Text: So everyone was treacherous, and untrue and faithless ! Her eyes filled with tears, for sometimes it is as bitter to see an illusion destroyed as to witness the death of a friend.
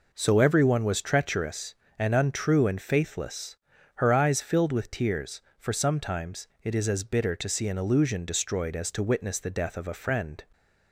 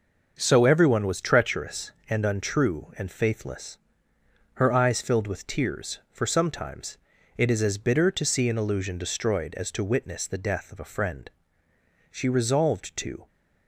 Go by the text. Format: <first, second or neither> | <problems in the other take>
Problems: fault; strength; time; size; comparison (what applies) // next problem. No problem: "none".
first | starts louder than the rest; until 1.3 s; 6.5 dB // pauses between "sometimes" and "it"; at 6.9 s; 0.40 s long // goes on to say "She resolved to"; noticeable; from 12.1 s on; 1.1 s long